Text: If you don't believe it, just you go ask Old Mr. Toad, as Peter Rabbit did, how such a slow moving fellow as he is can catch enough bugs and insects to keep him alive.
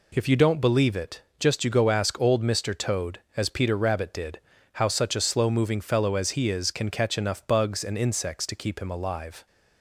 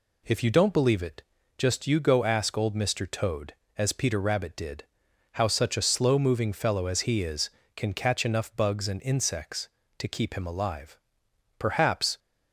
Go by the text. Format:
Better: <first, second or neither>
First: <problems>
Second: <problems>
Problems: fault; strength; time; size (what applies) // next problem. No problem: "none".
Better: first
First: none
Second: goes on to say "Perhaps"; from 11.5 s on; 0.60 s long